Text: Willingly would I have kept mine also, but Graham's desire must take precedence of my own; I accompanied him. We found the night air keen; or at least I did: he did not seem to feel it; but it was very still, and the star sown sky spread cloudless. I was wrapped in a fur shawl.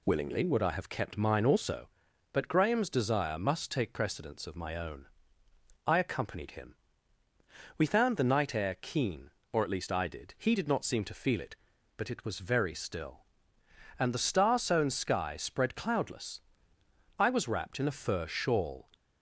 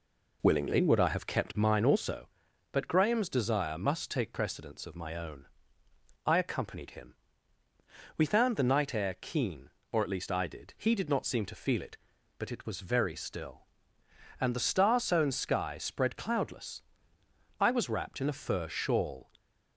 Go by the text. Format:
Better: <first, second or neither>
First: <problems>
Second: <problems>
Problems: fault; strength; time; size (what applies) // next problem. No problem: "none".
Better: first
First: none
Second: starts louder than the rest; until 1.7 s; 3.5 dB